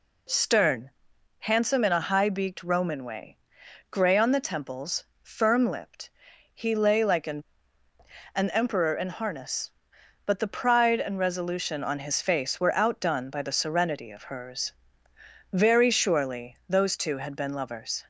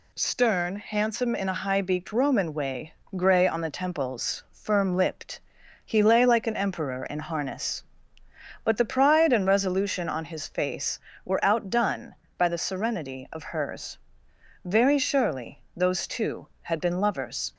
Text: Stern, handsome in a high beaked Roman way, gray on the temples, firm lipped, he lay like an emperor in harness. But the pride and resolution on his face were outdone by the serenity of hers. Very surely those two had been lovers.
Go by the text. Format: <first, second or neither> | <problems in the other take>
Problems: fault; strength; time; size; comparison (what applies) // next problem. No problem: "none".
second | says "an" twice; at 8.3 s